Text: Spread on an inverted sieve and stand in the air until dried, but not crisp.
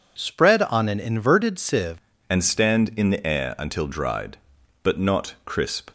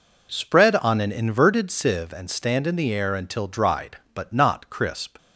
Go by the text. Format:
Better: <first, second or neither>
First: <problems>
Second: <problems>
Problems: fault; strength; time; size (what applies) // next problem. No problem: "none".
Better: second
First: changes voice at "and"; from 2.2 s on; 3.7 s long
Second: none